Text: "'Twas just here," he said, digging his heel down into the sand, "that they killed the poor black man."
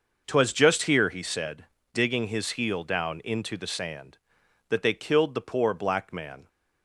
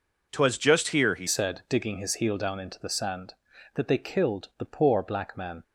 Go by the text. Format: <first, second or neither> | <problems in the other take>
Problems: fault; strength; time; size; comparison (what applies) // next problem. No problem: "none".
first | changes voice at "said"; from 1.2 s on; 4.4 s long